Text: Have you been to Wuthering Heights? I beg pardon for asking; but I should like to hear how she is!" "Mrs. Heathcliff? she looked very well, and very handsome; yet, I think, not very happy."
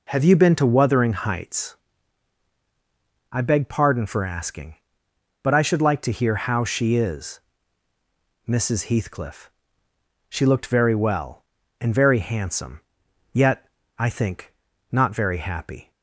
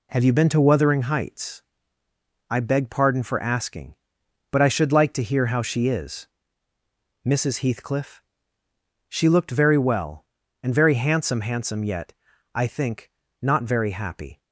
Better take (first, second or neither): first